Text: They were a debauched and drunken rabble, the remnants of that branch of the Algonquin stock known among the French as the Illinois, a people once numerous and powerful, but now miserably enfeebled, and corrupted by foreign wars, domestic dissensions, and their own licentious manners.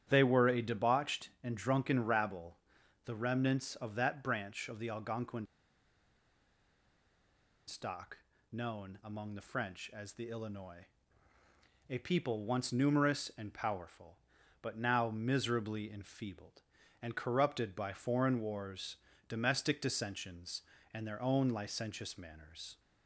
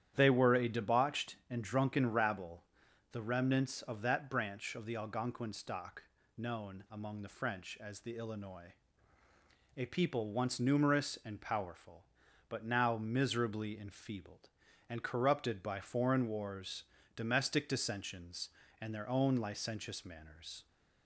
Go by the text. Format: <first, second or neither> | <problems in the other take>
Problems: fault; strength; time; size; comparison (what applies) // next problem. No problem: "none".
second | starts louder than the rest; strong; until 1.1 s; 10.5 dB; strong in the second // pauses between "Algonquin" and "stock"; strong; at 5.4 s; 2.2 s long // pauses between "stock" and "known"; slight; at 8.1 s; 0.34 s long; slight in the second